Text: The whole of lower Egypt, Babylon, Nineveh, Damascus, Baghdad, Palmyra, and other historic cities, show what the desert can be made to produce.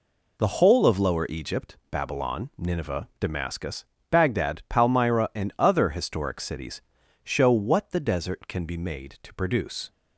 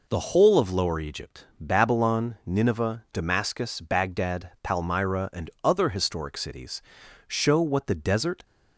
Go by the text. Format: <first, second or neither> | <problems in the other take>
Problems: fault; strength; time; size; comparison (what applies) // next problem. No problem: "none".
first | stops before "can be made to produce"; at 8.4 s